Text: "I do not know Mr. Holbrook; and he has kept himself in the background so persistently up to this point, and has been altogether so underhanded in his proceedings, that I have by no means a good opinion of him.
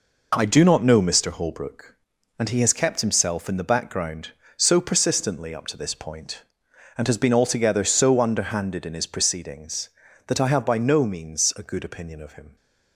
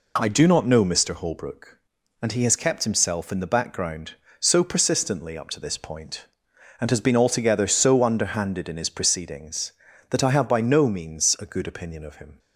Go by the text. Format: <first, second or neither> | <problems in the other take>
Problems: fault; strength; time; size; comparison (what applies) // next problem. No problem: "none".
second | gets quieter; strong; throughout; 7 dB